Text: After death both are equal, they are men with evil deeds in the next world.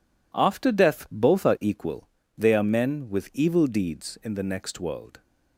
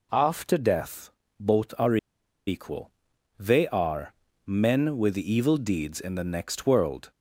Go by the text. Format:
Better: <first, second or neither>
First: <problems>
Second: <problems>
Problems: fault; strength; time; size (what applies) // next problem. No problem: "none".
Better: first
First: none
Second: pauses between "death" and "both"; slight; at 1.1 s; 0.26 s long // pauses between "are" and "equal"; noticeable; at 1.9 s; 0.50 s long // pauses between "are" and "men"; slight; at 4.1 s; 0.34 s long